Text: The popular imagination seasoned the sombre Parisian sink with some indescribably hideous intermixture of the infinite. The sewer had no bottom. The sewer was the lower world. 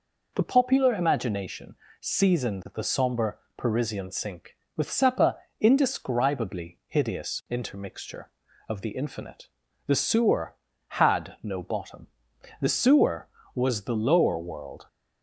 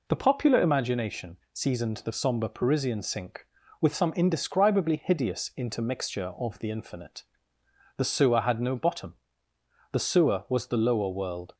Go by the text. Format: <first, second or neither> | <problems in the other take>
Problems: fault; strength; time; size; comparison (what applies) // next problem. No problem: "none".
second | pauses between "imagination" and "seasoned"; slight; at 1.7 s; 0.26 s long; slight in the second // pauses between "sombre" and "Parisian"; slight; at 3.3 s; 0.18 s long // says "sepa" for "some"; at 4.8 s